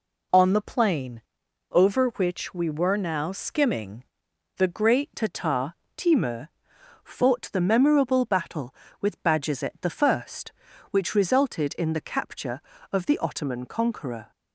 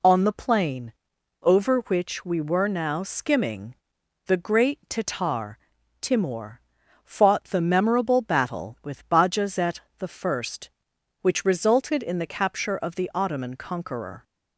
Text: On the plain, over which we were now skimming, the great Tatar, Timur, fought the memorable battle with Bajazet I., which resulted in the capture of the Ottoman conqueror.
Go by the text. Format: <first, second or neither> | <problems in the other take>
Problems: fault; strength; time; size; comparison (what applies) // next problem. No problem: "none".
second | changes voice at "Tatar"; from 5.1 s on; 9.2 s long